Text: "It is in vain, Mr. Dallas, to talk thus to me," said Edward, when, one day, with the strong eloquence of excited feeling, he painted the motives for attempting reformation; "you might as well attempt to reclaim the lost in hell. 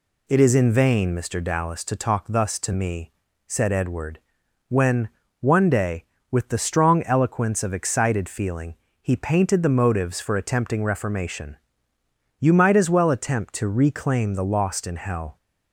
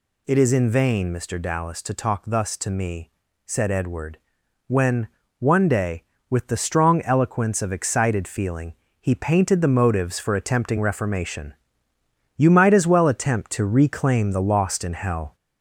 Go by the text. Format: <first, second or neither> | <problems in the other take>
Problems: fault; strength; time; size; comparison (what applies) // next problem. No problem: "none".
first | gets louder; slight; throughout; 2.5 dB